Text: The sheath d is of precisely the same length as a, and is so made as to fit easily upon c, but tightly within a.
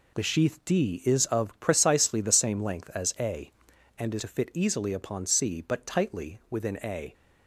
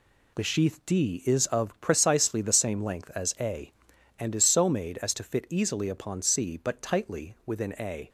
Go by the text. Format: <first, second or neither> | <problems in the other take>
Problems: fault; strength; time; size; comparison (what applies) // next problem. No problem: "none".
second | skips "so made as"; at 4.1 s